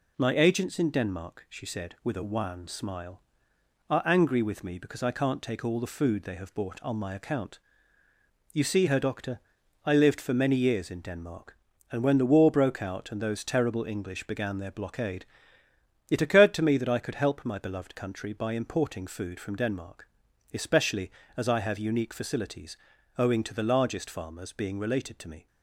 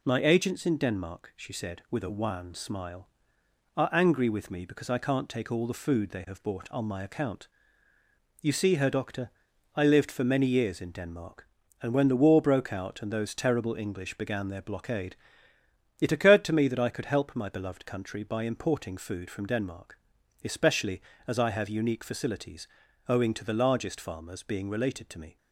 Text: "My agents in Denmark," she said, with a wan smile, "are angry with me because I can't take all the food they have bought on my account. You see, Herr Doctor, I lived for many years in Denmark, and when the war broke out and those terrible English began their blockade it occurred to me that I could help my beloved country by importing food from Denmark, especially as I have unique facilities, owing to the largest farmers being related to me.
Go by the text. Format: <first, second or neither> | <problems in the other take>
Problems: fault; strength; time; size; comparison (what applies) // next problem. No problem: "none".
neither | pauses between "blockade" and "it"; noticeable; the same in both